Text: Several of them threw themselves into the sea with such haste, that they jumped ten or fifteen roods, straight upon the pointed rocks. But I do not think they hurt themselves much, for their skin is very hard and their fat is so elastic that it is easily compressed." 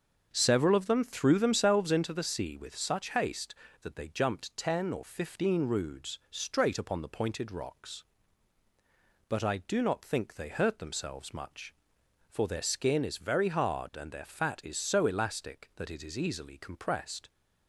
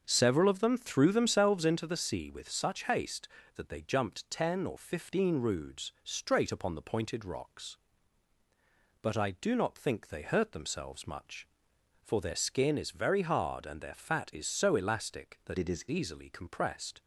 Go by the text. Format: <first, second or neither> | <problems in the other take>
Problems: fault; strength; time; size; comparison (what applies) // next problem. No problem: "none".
first | starts louder than the rest; until 1.0 s; 6.5 dB; also in the first // changes voice from "it" to "is"; from 15.5 to 15.8 s; 0.3 s long